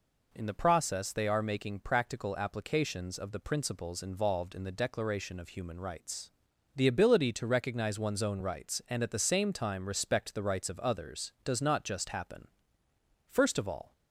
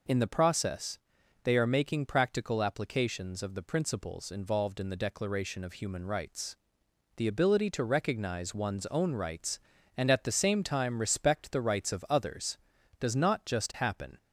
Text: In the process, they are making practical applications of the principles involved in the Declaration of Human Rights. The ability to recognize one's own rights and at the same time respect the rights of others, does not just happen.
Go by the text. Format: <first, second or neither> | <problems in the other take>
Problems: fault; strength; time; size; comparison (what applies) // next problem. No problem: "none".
second | goes on to say "First of all"; noticeable; from 13.2 s on; 0.64 s long